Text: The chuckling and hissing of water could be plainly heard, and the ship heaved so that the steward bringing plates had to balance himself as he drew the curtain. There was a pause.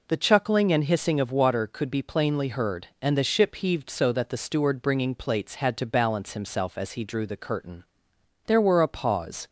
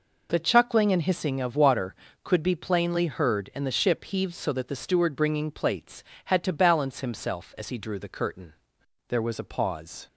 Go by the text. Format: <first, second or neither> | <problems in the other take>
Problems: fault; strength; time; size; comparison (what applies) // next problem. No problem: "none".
second | says "were" for "was"; at 8.5 s